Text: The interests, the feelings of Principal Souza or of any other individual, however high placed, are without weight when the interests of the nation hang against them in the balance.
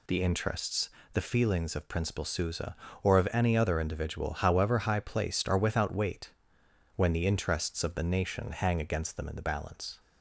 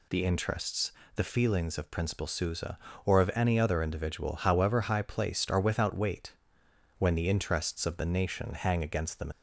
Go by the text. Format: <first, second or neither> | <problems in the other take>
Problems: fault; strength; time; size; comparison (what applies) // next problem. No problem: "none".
first | pauses between "weight" and "when"; noticeable; at 6.3 s; 0.66 s long; noticeable in the first // stops before "in the balance"; at 9.3 s